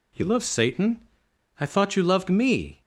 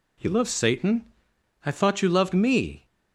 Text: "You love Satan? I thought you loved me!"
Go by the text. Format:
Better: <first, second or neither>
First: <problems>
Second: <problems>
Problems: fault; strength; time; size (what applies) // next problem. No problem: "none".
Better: neither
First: none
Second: none